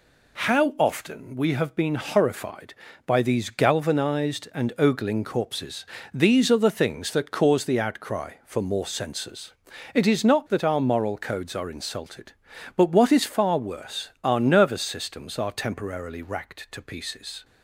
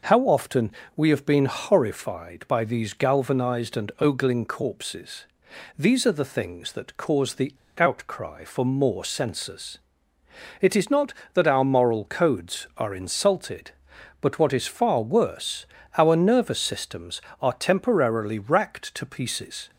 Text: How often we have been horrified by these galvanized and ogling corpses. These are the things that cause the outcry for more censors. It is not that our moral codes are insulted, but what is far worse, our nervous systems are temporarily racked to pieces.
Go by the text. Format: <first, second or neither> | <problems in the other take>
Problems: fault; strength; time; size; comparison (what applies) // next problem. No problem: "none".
first | pauses between "often" and "we"; slight; at 0.6 s; 0.28 s long // pauses between "the" and "outcry"; slight; at 7.5 s; 0.22 s long